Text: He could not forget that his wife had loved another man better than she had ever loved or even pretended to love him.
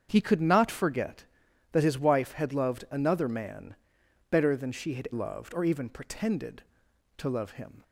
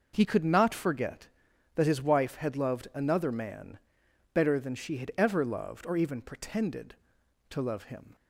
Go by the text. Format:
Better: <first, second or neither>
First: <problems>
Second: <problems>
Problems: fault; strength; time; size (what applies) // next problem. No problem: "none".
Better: second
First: starts louder than the rest; strong; until 1.1 s; 7.5 dB // pauses between "man" and "better"; noticeable; at 3.7 s; 0.56 s long // skips "ever"; at 5.0 s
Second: pauses between "man" and "better"; noticeable; at 3.7 s; 0.56 s long